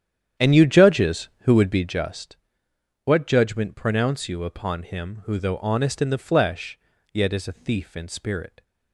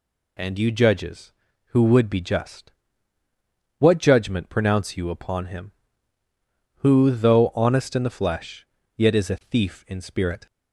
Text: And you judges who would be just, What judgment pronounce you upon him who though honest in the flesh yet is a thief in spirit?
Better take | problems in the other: second | starts louder than the rest; strong; until 2.1 s; 9.5 dB // pauses between "flesh" and "yet"; slight; at 6.7 s; 0.34 s long; slight in the second

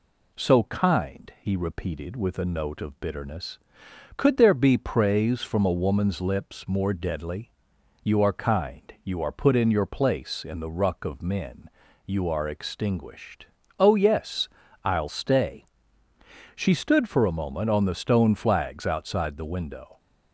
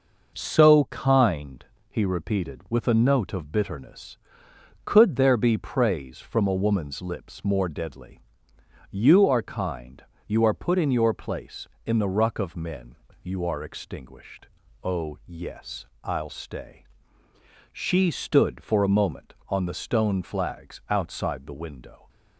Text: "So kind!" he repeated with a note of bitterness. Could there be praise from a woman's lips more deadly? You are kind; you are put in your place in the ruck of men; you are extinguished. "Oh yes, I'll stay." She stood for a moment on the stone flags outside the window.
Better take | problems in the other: neither | none

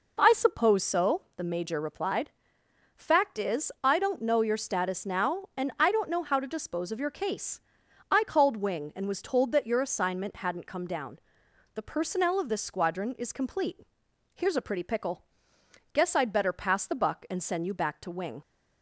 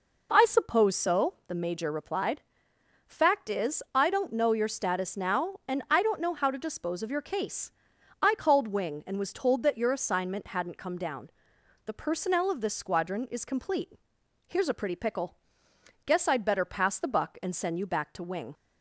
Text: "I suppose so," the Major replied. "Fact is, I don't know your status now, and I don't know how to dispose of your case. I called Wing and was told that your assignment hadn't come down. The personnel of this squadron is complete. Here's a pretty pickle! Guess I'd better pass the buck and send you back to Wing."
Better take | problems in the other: neither | none

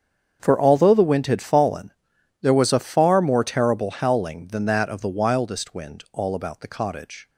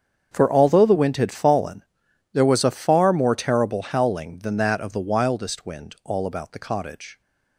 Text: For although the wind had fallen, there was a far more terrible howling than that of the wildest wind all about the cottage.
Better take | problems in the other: neither | starts louder than the rest; strong; the same in both

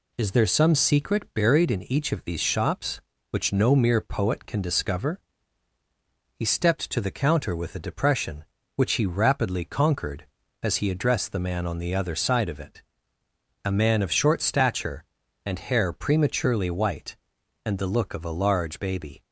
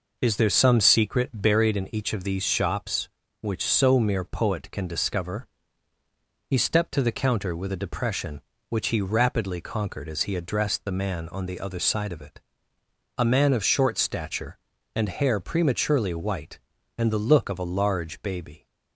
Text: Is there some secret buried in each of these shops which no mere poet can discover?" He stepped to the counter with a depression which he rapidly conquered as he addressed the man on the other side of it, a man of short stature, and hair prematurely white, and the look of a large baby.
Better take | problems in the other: first | says "so" for "no"; at 3.6 s

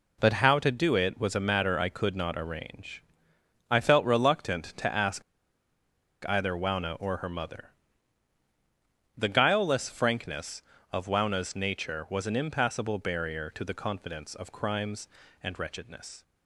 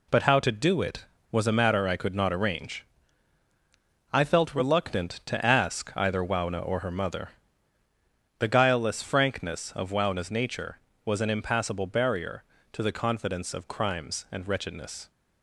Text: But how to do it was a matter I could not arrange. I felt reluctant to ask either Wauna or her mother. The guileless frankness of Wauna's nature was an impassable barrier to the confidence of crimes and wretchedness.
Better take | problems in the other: second | pauses between "ask" and "either"; at 5.2 s; 1.0 s long

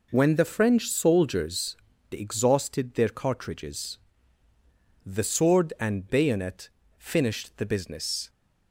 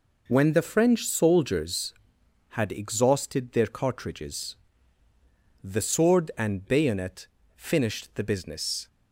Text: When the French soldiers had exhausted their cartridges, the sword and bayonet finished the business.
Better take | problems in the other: second | skips "had"; at 1.9 s // pauses between "bayonet" and "finished"; slight; at 6.6 s; 0.28 s long; slight in the second

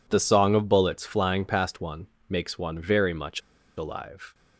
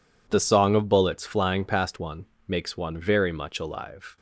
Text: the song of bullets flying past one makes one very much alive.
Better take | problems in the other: second | pauses between "one" and "makes"; slight; at 2.0 s; 0.24 s long; slight in the second // pauses between "much" and "alive"; at 3.4 s; 0.37 s long

